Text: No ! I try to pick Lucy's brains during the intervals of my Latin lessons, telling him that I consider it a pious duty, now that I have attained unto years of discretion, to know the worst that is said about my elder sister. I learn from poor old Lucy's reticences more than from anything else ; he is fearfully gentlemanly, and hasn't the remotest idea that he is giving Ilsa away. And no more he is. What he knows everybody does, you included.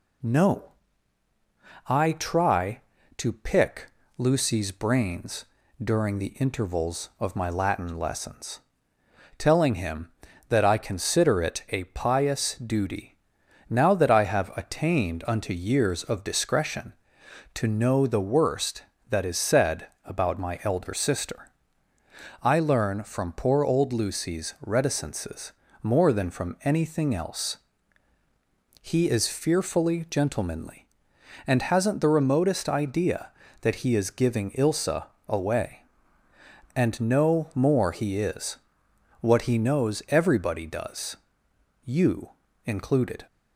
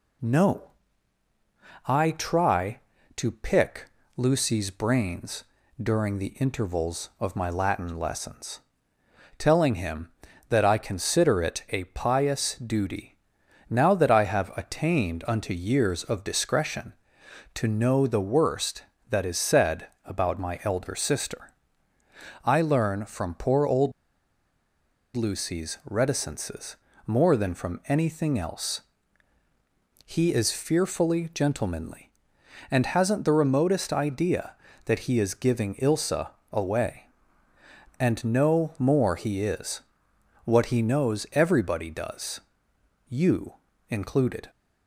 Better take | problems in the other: first | pauses between "pick" and "Lucy's"; slight; at 3.8 s; 0.26 s long; slight in the first // pauses between "brains" and "during"; at 5.4 s; 0.38 s long; also in the first // pauses between "said" and "about"; slight; at 19.8 s; 0.16 s long; slight in the first // pauses between "old" and "Lucy's"; at 23.9 s; 1.2 s long // pauses between "reticences" and "more"; slight; at 26.7 s; 0.30 s long; slight in the first // pauses between "Ilsa" and "away"; slight; at 36.2 s; 0.22 s long; slight in the first // pauses between "you" and "included"; slight; at 43.5 s; 0.36 s long; slight in the first

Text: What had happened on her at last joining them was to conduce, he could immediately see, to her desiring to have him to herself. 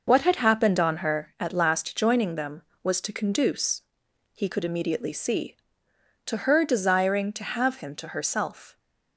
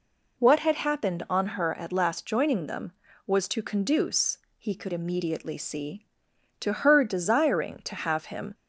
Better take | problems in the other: first | stops before "to herself"; at 8.5 s

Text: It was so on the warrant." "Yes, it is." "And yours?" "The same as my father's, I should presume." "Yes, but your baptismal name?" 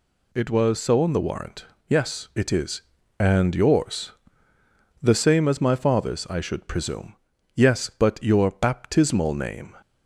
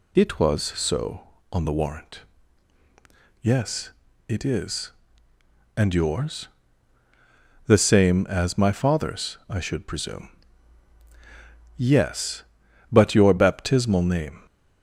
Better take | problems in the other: neither | none

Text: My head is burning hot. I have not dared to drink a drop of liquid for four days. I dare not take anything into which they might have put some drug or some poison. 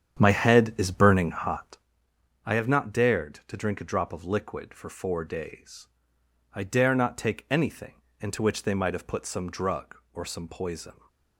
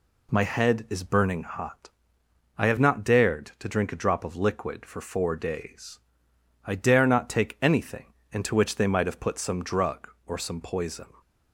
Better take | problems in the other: second | starts louder than the rest; strong; until 1.9 s; 8.5 dB // pauses between "anything" and "into"; slight; at 8.0 s; 0.18 s long; slight in the second

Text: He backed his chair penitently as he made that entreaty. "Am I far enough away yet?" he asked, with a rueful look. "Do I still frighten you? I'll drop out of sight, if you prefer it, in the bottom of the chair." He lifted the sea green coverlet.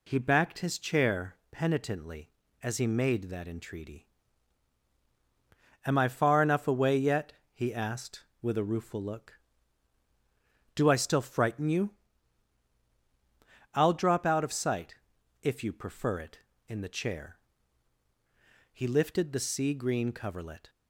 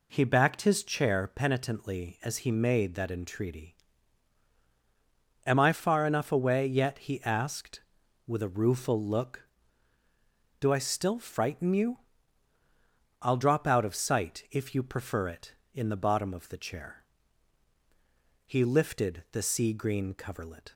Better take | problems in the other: second | pauses between "chair" and "penitently"; slight; at 1.3 s; 0.16 s long // skips "the bottom of"; at 16.7 s

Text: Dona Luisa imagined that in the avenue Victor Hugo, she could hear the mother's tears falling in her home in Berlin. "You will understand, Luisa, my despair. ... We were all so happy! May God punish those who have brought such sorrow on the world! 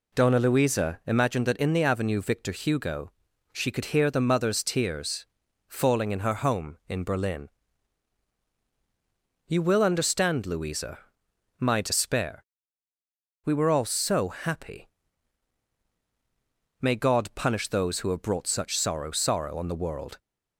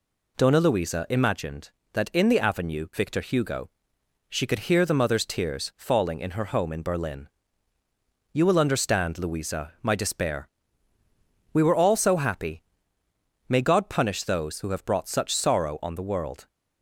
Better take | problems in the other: second | pauses between "tears" and "falling"; at 5.2 s; 0.40 s long // says "sorrow" twice; at 19.1 s

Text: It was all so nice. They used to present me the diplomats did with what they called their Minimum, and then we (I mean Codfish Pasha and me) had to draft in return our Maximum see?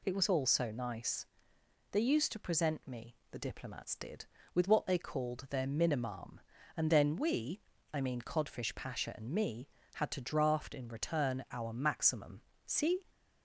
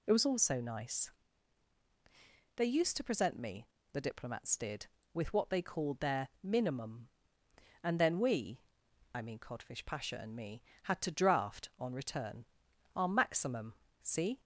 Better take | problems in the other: first | pauses between "me" and "the"; slight; at 3.6 s; 0.26 s long; slight in the first // says "on" for "in"; at 11.7 s // pauses between "return" and "our"; noticeable; at 12.4 s; 0.50 s long // pauses between "Maximum" and "see"; slight; at 13.7 s; 0.28 s long; slight in the first

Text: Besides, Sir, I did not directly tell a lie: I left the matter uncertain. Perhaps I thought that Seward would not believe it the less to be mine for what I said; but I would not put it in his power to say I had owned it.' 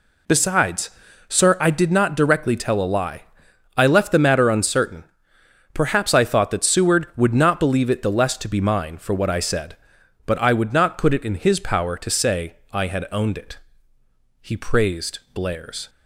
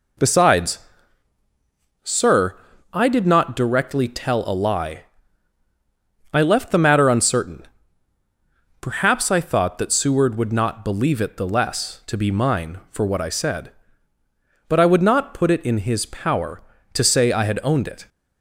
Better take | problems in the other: second | pauses between "say" and "I"; slight; at 12.5 s; 0.16 s long // goes on to say "He praised Blair's"; from 14.4 s on; 1.4 s long

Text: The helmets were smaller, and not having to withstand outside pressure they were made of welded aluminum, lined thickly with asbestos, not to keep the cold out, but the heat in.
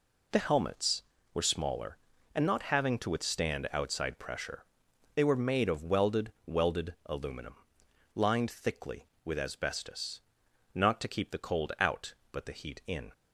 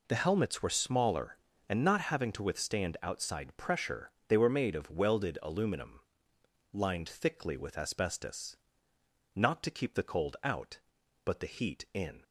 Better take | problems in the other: second | pauses between "pressure" and "they"; noticeable; at 4.6 s; 0.50 s long; slight in the second // says "welded" twice; at 6.4 s

